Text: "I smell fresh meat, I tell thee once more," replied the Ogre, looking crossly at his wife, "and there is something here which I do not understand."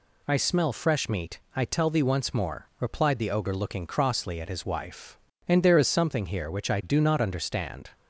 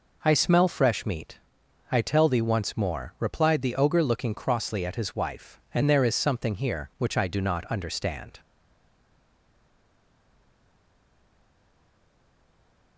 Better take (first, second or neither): first